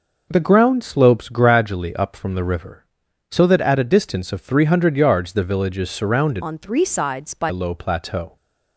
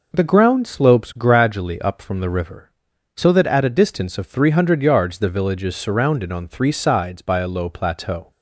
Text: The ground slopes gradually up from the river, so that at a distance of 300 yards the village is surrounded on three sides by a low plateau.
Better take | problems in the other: second | changes voice from "on" to "by"; from 6.4 to 7.4 s; 1.0 s long

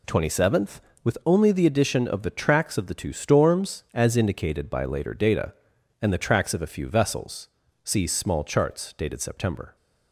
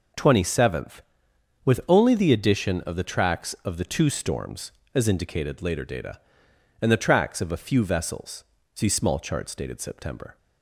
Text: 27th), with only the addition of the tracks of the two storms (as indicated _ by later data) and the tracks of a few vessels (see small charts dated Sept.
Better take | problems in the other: first | skips "by"; at 5.6 s

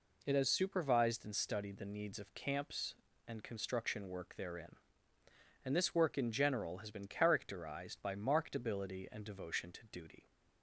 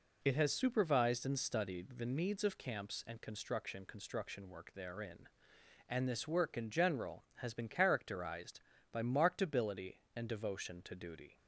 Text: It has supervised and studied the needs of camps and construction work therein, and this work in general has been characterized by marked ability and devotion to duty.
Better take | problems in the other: first | says "construction" twice; at 3.8 s

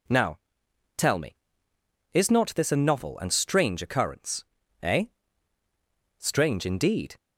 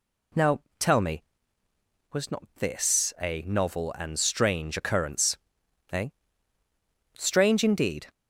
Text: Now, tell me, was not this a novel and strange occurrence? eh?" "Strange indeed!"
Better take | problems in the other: second | says "is" for "was"; at 2.1 s

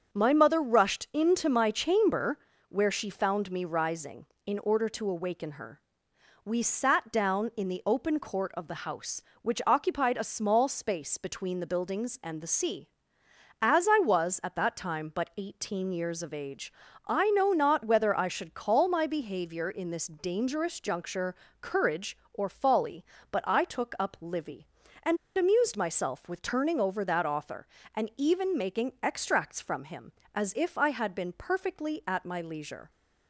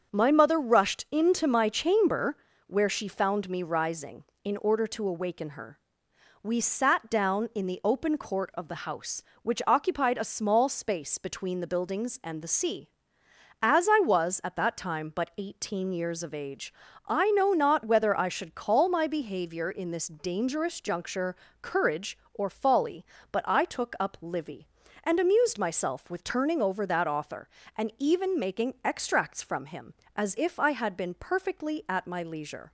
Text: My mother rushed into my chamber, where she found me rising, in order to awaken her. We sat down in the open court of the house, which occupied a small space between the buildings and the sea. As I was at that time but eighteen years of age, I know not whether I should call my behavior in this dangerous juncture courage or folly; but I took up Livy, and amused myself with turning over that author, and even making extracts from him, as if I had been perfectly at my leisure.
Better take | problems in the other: second | starts louder than the rest; strong; until 1.1 s; 7 dB; also in the second // pauses between "juncture" and "courage"; slight; at 21.3 s; 0.26 s long; slight in the second // pauses between "and" and "amused"; slight; at 25.1 s; 0.21 s long

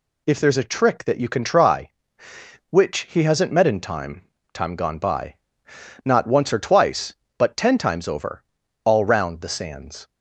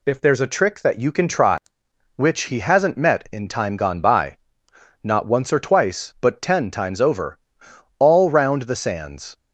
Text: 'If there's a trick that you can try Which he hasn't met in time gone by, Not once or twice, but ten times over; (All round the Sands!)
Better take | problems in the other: second | says "time" twice; at 4.5 s

